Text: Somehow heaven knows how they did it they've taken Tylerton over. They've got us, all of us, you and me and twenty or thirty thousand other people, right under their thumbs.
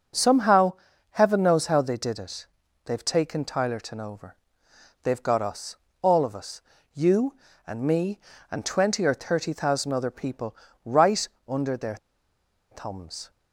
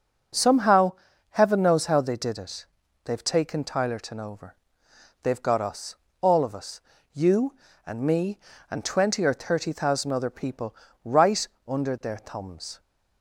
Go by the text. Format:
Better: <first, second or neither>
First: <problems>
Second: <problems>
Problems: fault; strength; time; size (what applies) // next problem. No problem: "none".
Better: second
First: pauses between "Somehow" and "heaven"; slight; at 0.7 s; 0.36 s long // pauses between "it" and "they've"; at 2.4 s; 0.40 s long // pauses between "right" and "under"; slight; at 11.2 s; 0.22 s long // pauses between "their" and "thumbs"; noticeable; at 11.9 s; 0.75 s long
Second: pauses between "Somehow" and "heaven"; slight; at 0.9 s; 0.36 s long // pauses between "it" and "they've"; at 2.6 s; 0.40 s long // pauses between "right" and "under"; slight; at 11.4 s; 0.22 s long